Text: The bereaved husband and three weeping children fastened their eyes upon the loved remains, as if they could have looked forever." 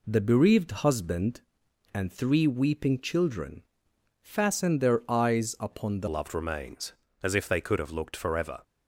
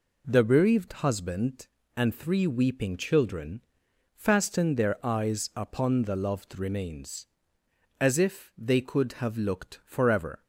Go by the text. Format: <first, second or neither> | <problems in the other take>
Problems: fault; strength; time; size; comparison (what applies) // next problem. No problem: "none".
second | pauses between "children" and "fastened"; noticeable; at 3.6 s; 0.58 s long; noticeable in the second // changes voice at "loved"; from 6.0 s on; 2.6 s long